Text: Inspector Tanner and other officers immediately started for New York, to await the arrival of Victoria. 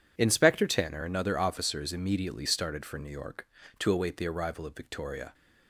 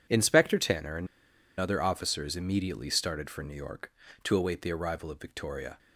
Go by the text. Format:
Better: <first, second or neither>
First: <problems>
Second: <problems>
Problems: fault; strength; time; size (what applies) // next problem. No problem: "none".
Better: first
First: none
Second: pauses between "and" and "other"; noticeable; at 1.0 s; 0.53 s long